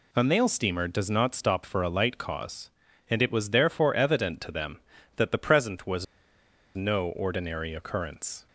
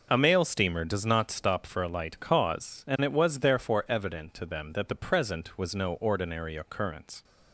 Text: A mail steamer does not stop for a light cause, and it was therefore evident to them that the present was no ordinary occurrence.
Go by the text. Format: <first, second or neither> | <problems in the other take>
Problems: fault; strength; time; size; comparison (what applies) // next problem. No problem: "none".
second | pauses between "was" and "no"; noticeable; at 6.0 s; 0.70 s long